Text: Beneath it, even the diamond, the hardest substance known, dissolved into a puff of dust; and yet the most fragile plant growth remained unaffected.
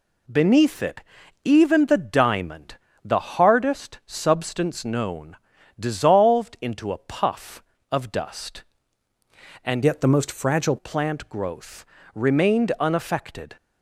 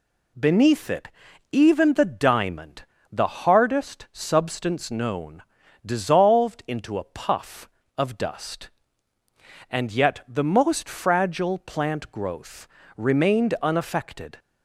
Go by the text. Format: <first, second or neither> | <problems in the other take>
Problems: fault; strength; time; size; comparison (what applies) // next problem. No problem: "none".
second | changes voice from "yet" to "fragile"; from 9.8 to 10.7 s; 0.9 s long // pauses between "growth" and "remained"; slight; at 11.8 s; 0.30 s long; slight in the second